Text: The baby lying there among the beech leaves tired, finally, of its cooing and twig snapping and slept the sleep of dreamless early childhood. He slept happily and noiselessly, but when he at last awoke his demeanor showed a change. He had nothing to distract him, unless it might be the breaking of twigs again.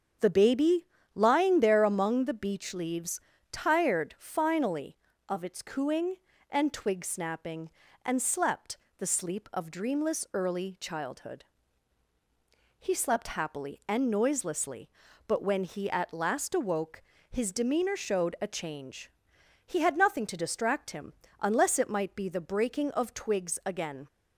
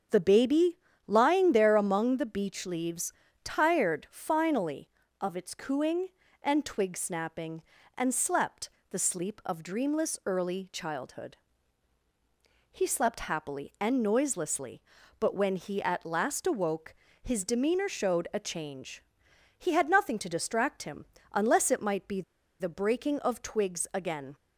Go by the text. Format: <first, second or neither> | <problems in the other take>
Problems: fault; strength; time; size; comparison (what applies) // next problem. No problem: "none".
first | starts louder than the rest; until 1.4 s; 7 dB; strong in the first // pauses between "baby" and "lying"; slight; at 0.7 s; 0.30 s long; slight in the first // pauses between "leaves" and "tired"; slight; at 3.1 s; 0.30 s long; slight in the first // pauses between "slept" and "the"; slight; at 8.6 s; 0.22 s long; slight in the first // pauses between "awoke" and "his"; slight; at 16.9 s; 0.26 s long; slight in the first // pauses between "be" and "the"; at 22.2 s; 0.38 s long